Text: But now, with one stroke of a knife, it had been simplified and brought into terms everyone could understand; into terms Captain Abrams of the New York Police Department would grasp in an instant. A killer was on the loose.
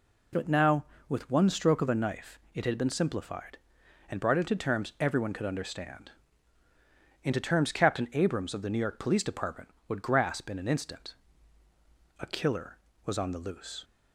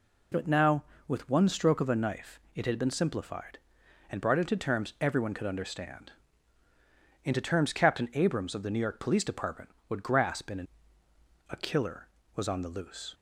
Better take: first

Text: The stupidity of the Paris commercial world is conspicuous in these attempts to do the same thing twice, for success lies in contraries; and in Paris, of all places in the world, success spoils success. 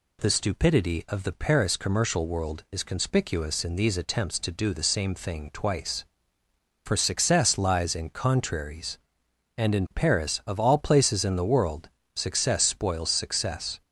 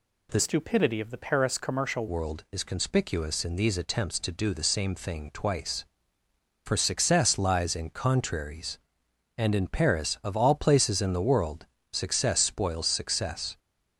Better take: first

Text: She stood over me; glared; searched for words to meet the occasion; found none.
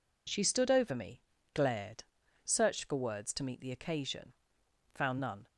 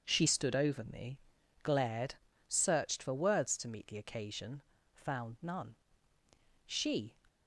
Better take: first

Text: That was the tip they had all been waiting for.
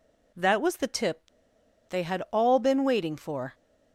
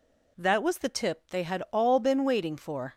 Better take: second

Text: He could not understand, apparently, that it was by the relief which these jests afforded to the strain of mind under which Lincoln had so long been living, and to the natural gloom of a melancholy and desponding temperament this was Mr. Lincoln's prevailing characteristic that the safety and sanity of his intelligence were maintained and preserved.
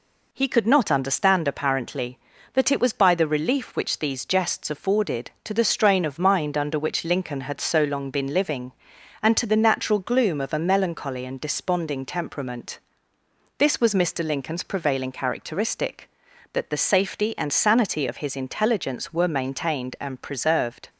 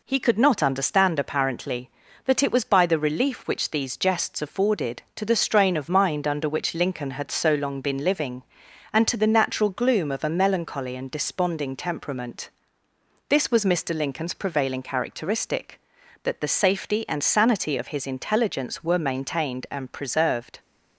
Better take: neither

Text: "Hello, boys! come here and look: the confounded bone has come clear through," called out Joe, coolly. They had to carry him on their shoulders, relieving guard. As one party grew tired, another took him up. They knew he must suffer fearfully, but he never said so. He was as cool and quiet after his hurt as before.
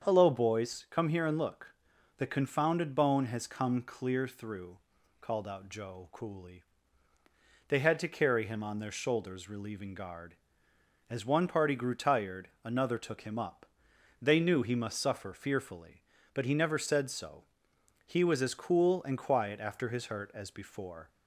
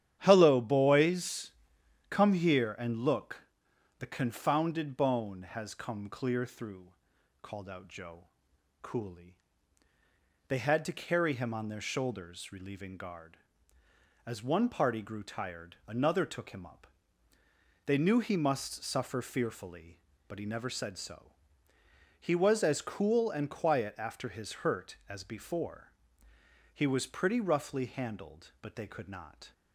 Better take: first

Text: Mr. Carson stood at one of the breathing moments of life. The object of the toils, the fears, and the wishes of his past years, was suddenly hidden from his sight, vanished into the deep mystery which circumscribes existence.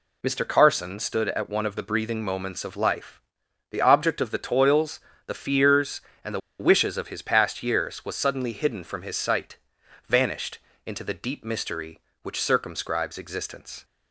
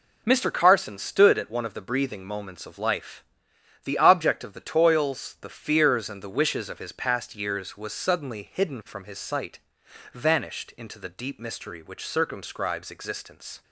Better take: second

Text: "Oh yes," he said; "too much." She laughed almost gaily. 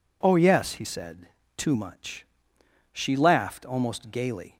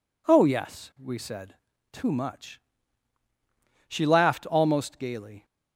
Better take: first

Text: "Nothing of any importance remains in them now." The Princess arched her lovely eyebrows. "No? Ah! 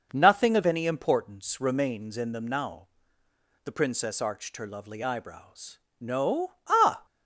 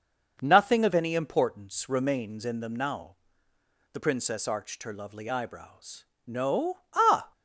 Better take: neither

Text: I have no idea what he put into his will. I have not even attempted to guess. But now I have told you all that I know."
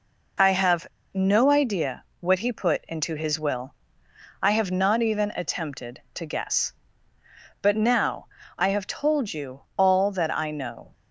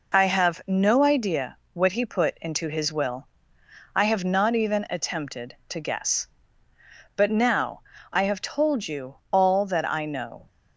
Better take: second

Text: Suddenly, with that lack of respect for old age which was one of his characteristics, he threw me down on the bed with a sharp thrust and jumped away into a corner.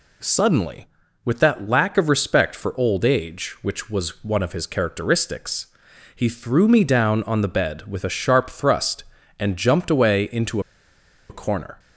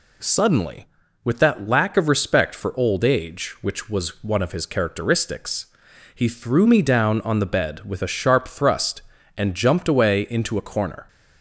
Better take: second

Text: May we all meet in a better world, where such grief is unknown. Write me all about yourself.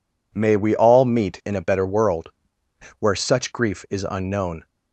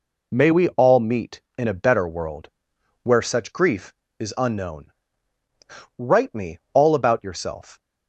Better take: second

